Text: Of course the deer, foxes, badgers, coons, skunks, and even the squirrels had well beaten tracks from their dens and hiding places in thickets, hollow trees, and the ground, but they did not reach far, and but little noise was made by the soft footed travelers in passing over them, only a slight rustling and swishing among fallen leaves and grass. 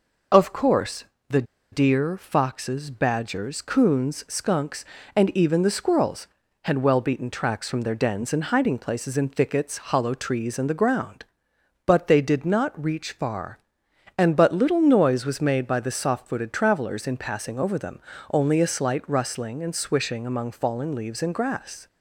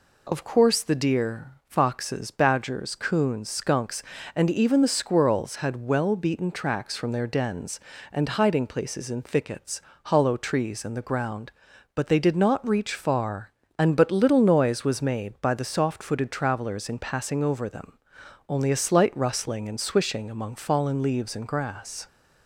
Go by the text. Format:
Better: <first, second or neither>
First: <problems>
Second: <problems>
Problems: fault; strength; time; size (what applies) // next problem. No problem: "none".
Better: second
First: pauses between "course" and "the"; slight; at 1.0 s; 0.24 s long // pauses between "the" and "deer"; slight; at 1.4 s; 0.28 s long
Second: none